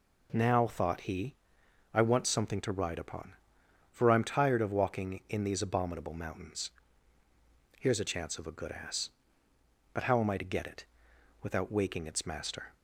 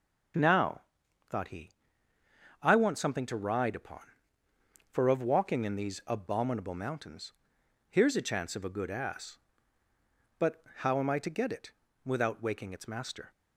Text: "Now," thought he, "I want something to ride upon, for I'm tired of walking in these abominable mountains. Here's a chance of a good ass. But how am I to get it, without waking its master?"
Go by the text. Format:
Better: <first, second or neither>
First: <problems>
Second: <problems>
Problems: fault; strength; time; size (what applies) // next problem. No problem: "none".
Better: first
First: none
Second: starts louder than the rest; strong; until 2.7 s; 7.5 dB // skips "I'm tired"; at 5.0 s // pauses between "But" and "how"; slight; at 10.6 s; 0.18 s long